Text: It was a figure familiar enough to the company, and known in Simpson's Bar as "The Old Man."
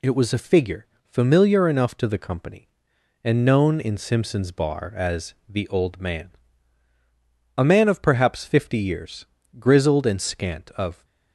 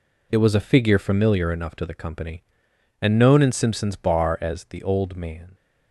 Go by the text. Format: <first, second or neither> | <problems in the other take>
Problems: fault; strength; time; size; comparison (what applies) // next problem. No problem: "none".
second | pauses between "figure" and "familiar"; slight; at 0.8 s; 0.18 s long // goes on to say "A man of perhaps fifty years grizzled and scant of"; strong; from 7.5 s on; 3.4 s long